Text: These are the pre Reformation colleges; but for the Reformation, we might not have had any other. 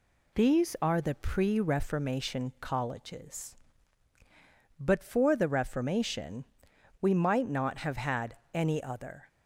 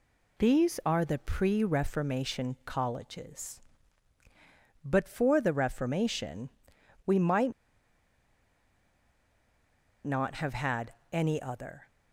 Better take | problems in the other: first | pauses between "might" and "not"; strong; at 7.5 s; 2.5 s long // pauses between "had" and "any"; slight; at 10.9 s; 0.18 s long; slight in the first

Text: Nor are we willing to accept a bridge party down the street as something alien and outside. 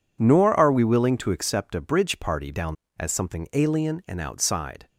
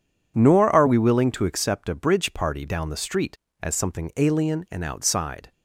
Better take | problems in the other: second | skips "the street"; at 2.8 s

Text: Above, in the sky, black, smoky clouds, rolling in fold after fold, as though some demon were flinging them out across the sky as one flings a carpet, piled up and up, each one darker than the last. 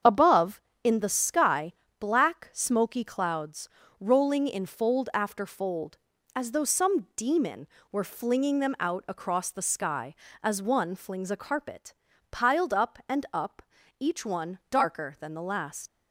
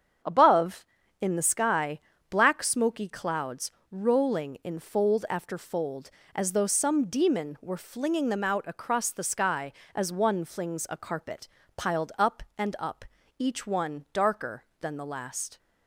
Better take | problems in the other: second | starts louder than the rest; strong; until 1.2 s; 7.5 dB; strong in the second // leaves "last" unfinished; at 15.8 s; 65 ms

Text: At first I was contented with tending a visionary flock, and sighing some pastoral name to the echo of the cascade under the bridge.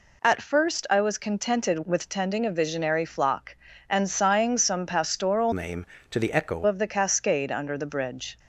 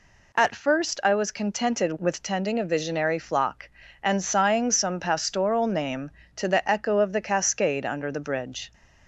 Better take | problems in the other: second | changes voice from "name" to "echo"; from 5.5 to 6.6 s; 1.1 s long

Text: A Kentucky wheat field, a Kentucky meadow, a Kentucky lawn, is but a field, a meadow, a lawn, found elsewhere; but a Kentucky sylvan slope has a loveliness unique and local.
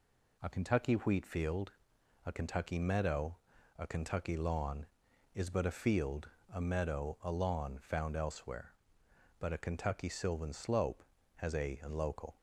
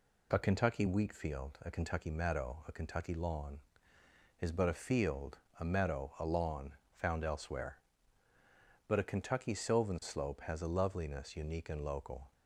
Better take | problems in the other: second | skips "loveliness unique"; at 11.7 s

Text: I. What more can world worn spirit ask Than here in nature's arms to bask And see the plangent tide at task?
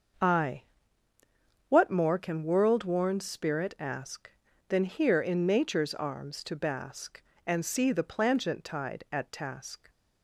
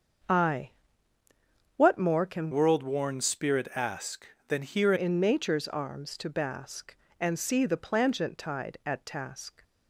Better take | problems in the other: first | starts louder than the rest; until 2.3 s; 7 dB; also in the first // changes voice from "world" to "here"; from 2.5 to 4.9 s; 2.4 s long

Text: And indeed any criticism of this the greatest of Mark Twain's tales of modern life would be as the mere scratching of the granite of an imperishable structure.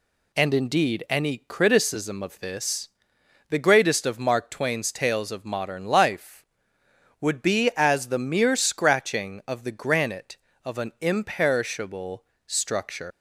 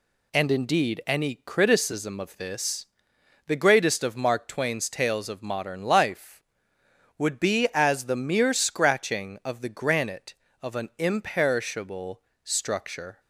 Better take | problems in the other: second | pauses between "this" and "the"; noticeable; at 2.8 s; 0.62 s long; noticeable in the second // pauses between "imperishable" and "structure"; slight; at 12.2 s; 0.22 s long; slight in the second // leaves "structure" unfinished; at 13.1 s; 115 ms

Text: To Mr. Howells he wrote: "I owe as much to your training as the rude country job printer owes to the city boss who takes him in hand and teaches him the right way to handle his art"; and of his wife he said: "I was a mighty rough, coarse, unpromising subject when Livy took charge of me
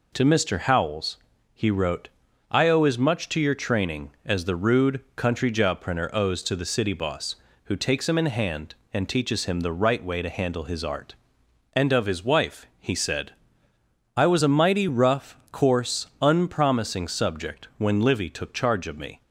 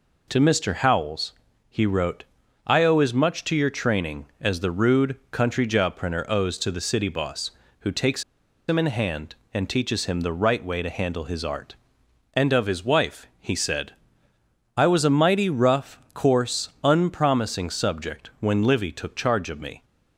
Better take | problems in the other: first | pauses between "Howells" and "he"; at 1.3 s; 0.38 s long; also in the first // pauses between "takes" and "him"; at 8.2 s; 0.45 s long

